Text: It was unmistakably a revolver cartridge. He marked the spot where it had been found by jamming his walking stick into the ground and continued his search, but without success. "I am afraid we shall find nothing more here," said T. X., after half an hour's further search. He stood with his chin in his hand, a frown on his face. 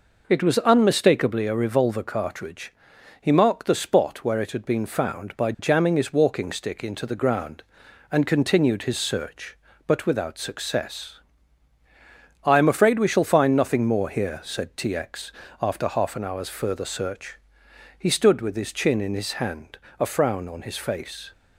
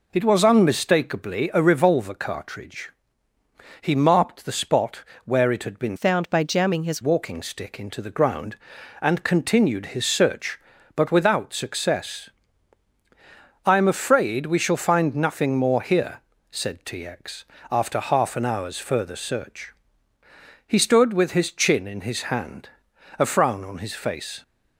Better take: first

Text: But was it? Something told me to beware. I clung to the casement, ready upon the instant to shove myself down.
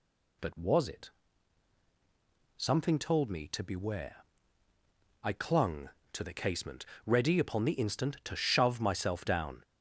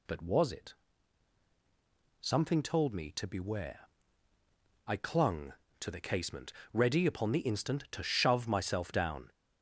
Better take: neither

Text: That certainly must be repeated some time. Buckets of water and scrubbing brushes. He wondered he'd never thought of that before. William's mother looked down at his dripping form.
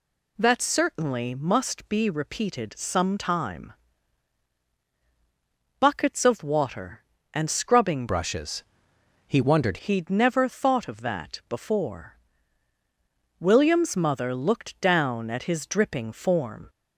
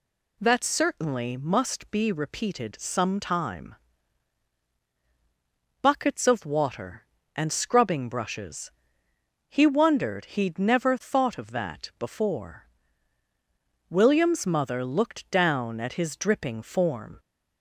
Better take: second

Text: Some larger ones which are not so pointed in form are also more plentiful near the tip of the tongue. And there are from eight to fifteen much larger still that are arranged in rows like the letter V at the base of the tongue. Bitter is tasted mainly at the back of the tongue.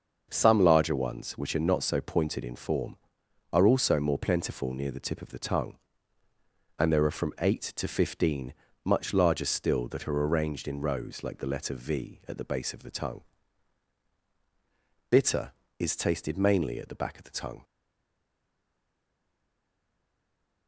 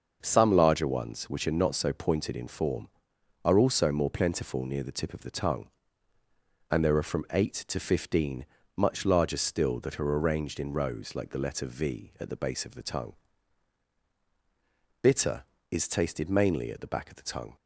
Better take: second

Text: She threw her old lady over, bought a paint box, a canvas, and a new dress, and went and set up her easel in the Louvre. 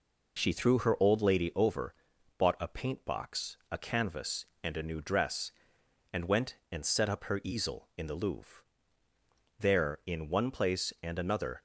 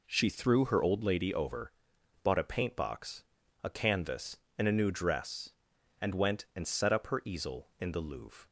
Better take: second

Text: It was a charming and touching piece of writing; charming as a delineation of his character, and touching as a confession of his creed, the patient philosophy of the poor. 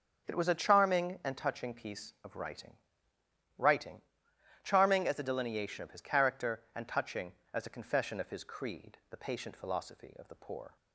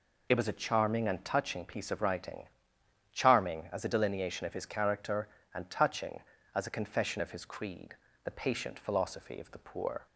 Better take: second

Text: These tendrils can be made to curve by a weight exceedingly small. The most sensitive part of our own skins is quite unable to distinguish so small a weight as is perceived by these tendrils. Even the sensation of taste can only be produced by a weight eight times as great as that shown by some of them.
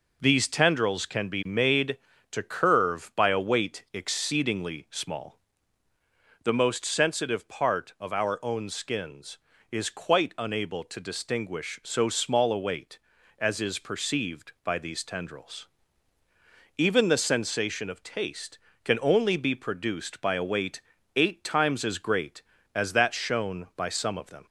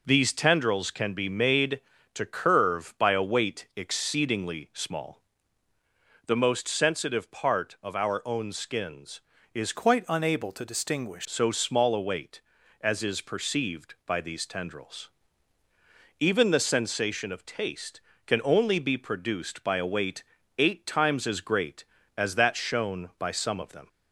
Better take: first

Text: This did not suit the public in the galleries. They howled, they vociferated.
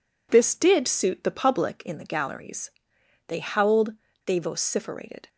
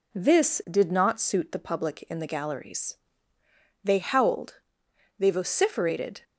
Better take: second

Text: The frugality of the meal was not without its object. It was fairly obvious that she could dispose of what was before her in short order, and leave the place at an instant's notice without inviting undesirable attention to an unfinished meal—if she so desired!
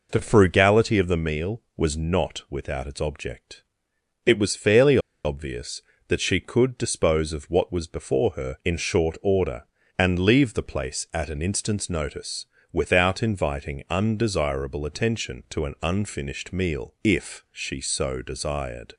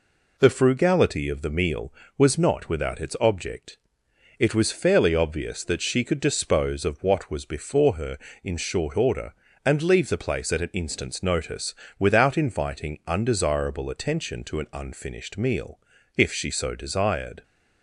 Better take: second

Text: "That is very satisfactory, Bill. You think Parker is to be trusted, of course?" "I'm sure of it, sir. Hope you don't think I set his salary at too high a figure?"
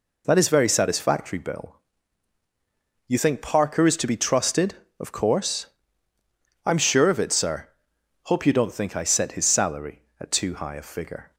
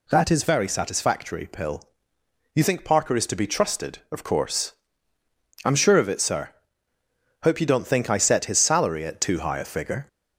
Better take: first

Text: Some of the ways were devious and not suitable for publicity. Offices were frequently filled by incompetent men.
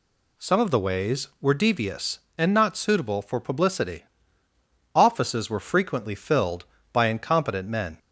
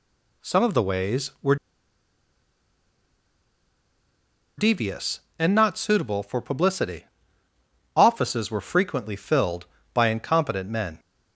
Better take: first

